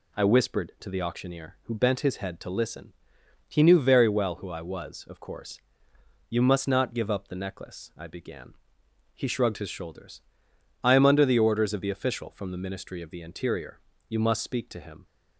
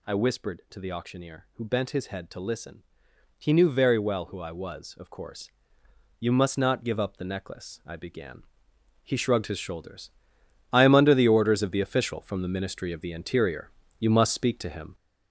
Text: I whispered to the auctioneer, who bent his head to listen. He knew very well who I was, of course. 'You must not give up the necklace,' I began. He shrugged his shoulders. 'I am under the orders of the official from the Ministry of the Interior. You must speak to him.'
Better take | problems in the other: first | gets louder; throughout; 6.5 dB

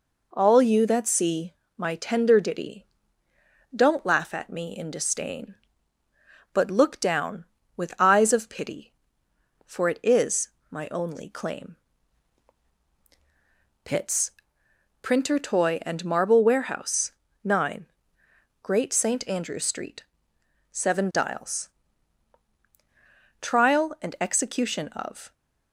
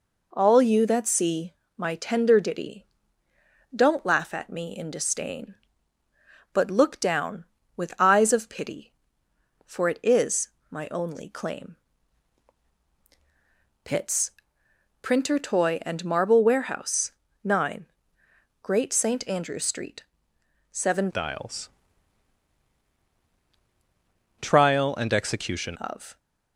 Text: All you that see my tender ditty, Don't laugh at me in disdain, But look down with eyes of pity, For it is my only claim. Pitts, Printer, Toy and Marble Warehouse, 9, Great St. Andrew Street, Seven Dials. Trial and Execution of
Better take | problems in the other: first | pauses between "see" and "my"; slight; at 1.5 s; 0.22 s long; slight in the first // pauses between "is" and "my"; slight; at 10.4 s; 0.20 s long; slight in the first // changes voice from "Dials" to "Execution"; from 21.1 to 25.7 s; 4.6 s long

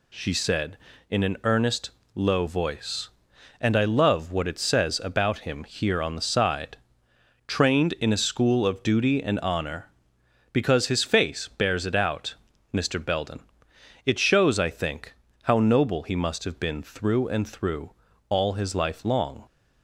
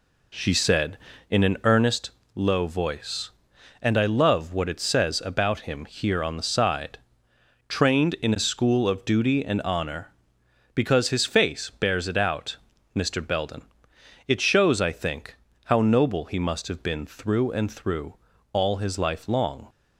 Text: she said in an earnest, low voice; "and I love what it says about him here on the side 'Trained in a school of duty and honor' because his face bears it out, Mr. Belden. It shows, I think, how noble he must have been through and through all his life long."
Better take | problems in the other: first | starts louder than the rest; slight; until 2.0 s; 3 dB // pauses between "side" and "Trained"; noticeable; at 6.9 s; 0.72 s long; noticeable in the first // pauses between "through" and "all"; slight; at 18.1 s; 0.36 s long; slight in the first

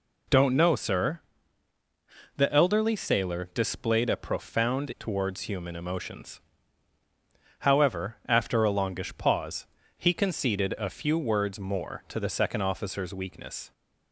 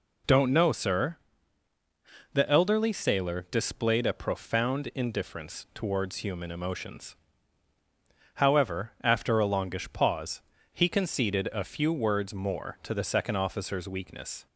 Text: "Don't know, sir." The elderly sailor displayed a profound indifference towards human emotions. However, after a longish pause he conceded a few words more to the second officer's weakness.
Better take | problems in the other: second | skips "indifference"; at 4.9 s // pauses between "pause" and "he"; slight; at 9.6 s; 0.32 s long; slight in the second

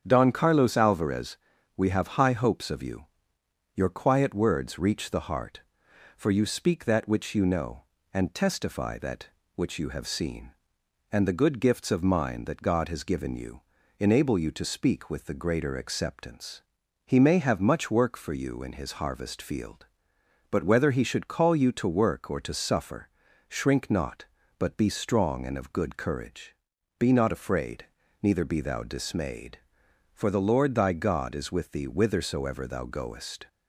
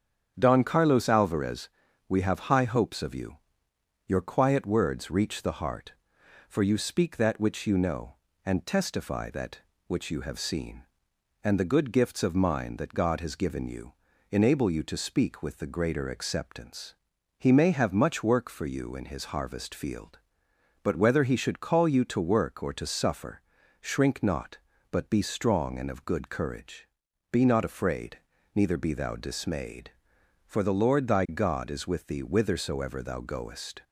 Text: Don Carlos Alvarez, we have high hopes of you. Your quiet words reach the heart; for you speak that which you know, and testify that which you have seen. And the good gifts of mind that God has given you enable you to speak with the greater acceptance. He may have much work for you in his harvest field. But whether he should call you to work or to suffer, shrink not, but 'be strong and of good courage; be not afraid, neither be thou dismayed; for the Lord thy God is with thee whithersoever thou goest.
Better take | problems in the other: neither | starts louder than the rest; strong; the same in both // pauses between "you" and "enable"; the same in both

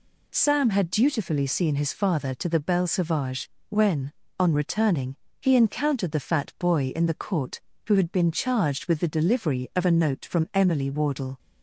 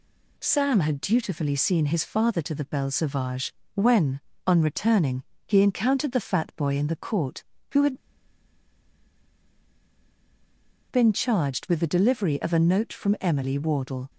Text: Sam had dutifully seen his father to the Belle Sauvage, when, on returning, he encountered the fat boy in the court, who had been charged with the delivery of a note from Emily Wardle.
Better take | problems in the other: first | pauses between "had" and "been"; strong; at 7.9 s; 2.9 s long

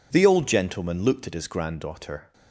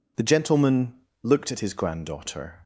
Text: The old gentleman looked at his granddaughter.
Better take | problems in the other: first | skips "old"; at 0.2 s // pauses between "gentleman" and "looked"; slight; at 0.9 s; 0.30 s long

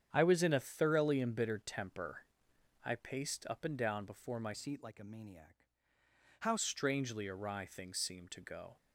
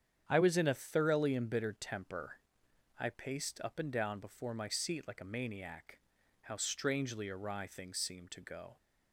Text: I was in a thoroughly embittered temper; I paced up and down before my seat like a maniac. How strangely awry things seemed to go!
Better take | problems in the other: second | starts louder than the rest; strong; until 1.1 s; 8.5 dB; strong in the second // changes voice from "seat" to "How"; from 4.5 to 6.5 s; 2.0 s long

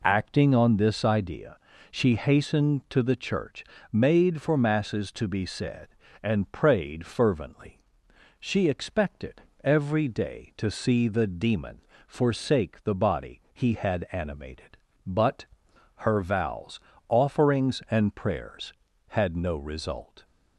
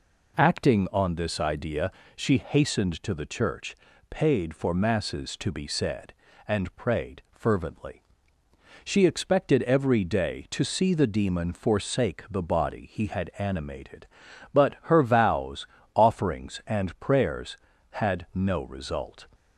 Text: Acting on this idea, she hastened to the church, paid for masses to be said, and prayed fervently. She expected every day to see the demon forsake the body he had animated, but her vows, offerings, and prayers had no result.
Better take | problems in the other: second | says "made" for "paid"; at 3.9 s // pauses between "expected" and "every"; slight; at 9.4 s; 0.20 s long // pauses between "demon" and "forsake"; slight; at 11.8 s; 0.26 s long // pauses between "but" and "her"; noticeable; at 15.4 s; 0.52 s long

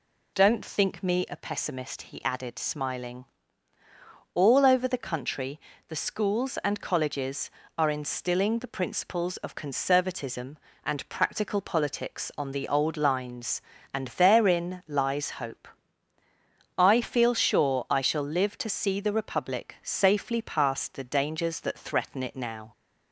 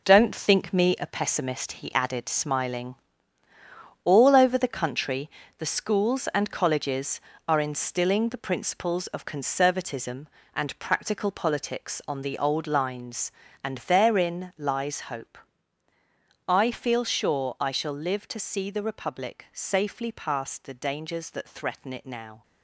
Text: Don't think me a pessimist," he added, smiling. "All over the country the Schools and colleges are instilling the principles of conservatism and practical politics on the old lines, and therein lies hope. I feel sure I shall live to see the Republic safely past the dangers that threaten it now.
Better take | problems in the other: first | gets quieter; strong; throughout; 8.5 dB // pauses between "country" and "the"; slight; at 5.2 s; 0.30 s long; slight in the first

